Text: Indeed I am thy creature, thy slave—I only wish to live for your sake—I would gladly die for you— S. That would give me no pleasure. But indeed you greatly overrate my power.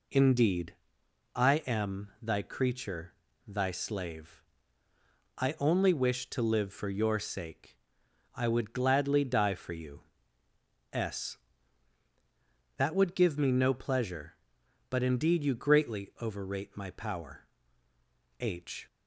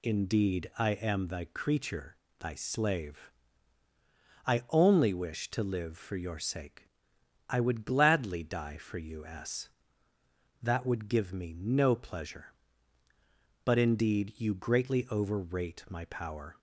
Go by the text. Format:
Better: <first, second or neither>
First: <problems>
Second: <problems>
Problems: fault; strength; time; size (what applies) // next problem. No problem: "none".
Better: second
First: pauses between "Indeed" and "I"; noticeable; at 0.7 s; 0.60 s long // goes on to say "H"; slight; from 18.3 s on; 0.48 s long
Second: none